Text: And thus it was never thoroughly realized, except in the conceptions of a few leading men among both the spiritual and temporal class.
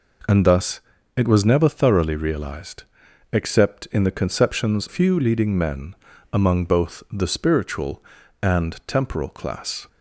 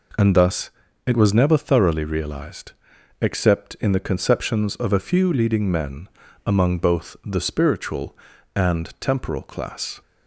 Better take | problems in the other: second | pauses between "thus" and "it"; slight; at 0.8 s; 0.36 s long; slight in the second // skips "of a"; at 4.8 s // pauses between "men" and "among"; slight; at 5.9 s; 0.36 s long; slight in the second

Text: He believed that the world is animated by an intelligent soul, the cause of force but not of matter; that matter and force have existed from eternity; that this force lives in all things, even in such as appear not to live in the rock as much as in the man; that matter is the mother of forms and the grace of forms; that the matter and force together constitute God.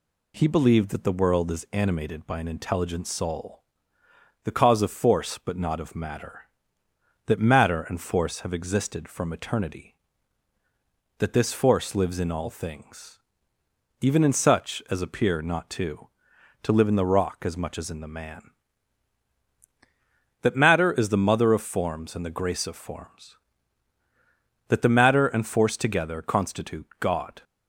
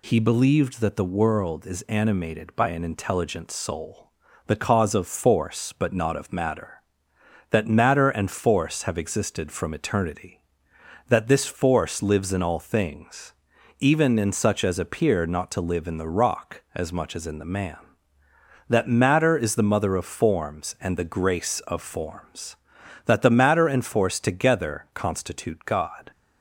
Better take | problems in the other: second | says "to" twice; at 16.6 s

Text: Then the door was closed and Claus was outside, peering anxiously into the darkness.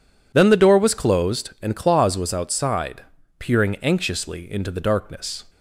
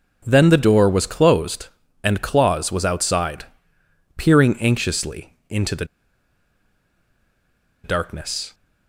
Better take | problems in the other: first | pauses between "the" and "darkness"; strong; at 5.8 s; 1.9 s long

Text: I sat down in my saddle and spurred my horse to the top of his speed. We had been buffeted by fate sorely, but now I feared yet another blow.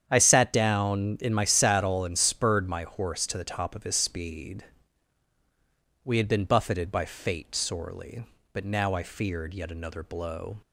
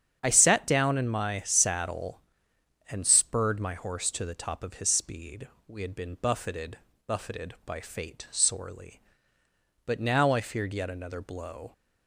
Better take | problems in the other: first | starts louder than the rest; strong; until 1.2 s; 8 dB; strong in the first // says "buffeted" twice; at 7.0 s

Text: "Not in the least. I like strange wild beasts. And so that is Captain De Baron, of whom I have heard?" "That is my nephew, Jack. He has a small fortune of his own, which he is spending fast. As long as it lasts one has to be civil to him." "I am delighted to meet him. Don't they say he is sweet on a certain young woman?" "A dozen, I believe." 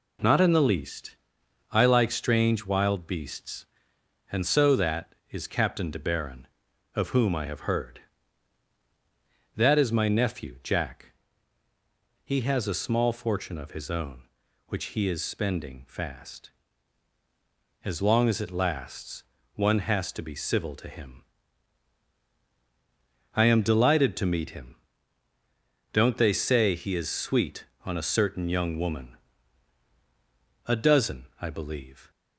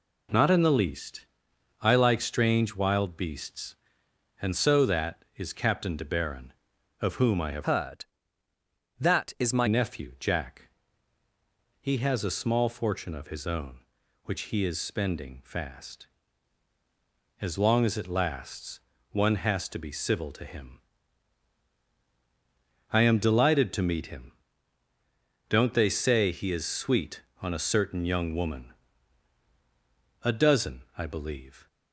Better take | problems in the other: first | changes voice from "heard" to "my"; from 7.6 to 9.6 s; 2.0 s long // pauses between "lasts" and "one"; slight; at 18.8 s; 0.32 s long; slight in the first

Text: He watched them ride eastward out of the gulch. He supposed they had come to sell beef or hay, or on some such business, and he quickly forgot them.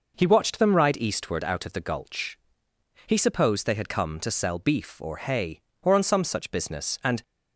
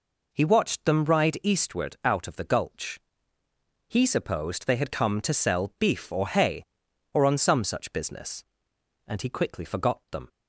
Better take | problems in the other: second | stops before "he quickly forgot them"; at 7.2 s

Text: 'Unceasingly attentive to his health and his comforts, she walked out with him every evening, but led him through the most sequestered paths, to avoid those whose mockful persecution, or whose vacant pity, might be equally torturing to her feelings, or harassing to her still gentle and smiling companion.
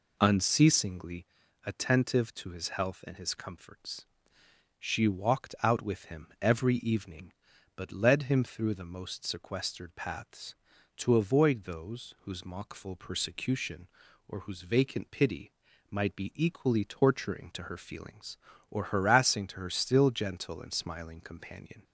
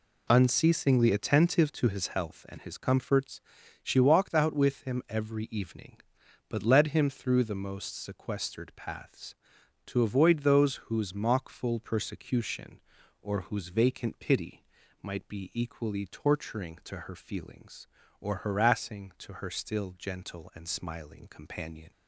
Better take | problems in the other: second | starts louder than the rest; until 1.3 s; 3.5 dB // pauses between "Unceasingly" and "attentive"; slight; at 1.2 s; 0.36 s long

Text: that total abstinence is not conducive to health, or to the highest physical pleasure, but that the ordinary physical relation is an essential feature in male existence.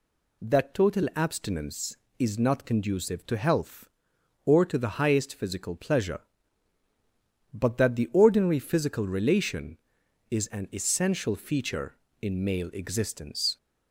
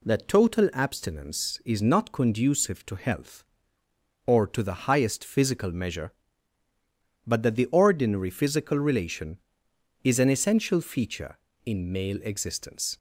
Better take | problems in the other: first | says "measure" for "pleasure"; at 5.7 s

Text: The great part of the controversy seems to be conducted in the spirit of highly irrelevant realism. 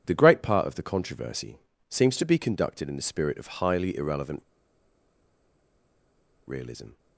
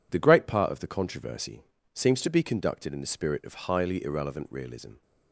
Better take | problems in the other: second | pauses between "controversy" and "seems"; slight; at 1.5 s; 0.32 s long; slight in the second // pauses between "irrelevant" and "realism"; strong; at 4.4 s; 2.0 s long

